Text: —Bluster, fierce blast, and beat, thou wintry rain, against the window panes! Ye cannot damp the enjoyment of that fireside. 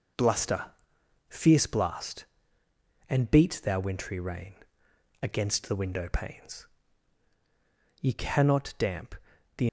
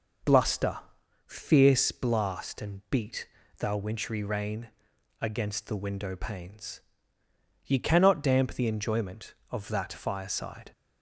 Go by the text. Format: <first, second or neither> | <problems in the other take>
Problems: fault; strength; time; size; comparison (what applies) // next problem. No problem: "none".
second | pauses between "damp" and "the"; at 9.1 s; 0.42 s long // stops before "enjoyment of that fireside"; at 9.6 s